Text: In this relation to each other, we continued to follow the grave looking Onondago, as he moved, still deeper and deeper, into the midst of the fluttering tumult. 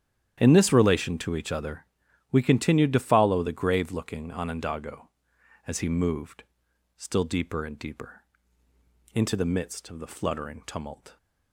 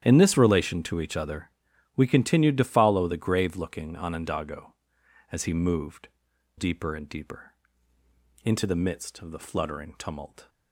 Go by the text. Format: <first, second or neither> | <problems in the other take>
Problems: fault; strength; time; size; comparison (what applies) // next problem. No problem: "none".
first | starts louder than the rest; strong; until 1.0 s; 10.5 dB; strong in the first // skips "still"; at 6.3 s